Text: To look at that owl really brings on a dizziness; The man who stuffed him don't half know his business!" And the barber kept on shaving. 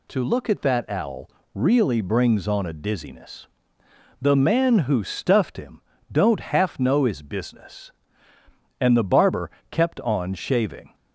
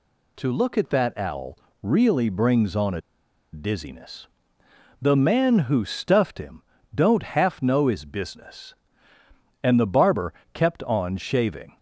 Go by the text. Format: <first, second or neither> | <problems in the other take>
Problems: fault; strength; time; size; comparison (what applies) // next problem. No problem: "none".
first | pauses between "owl" and "really"; slight; at 1.5 s; 0.24 s long; slight in the first // pauses between "a" and "dizziness"; noticeable; at 3.0 s; 0.52 s long // pauses between "him" and "don't"; slight; at 6.6 s; 0.32 s long; slight in the first // pauses between "barber" and "kept"; slight; at 10.3 s; 0.18 s long; slight in the first